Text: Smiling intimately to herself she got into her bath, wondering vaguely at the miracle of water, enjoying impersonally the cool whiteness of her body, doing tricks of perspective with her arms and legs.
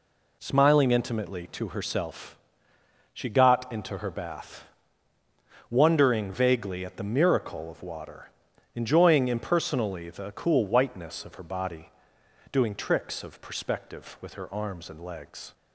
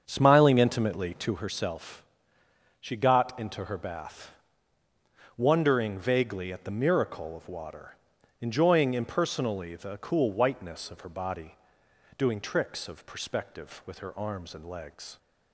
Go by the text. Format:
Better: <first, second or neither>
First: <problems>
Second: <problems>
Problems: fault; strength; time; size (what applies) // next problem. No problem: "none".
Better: first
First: pauses between "herself" and "she"; noticeable; at 2.3 s; 0.74 s long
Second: starts louder than the rest; strong; until 1.4 s; 7 dB // pauses between "herself" and "she"; noticeable; at 2.0 s; 0.74 s long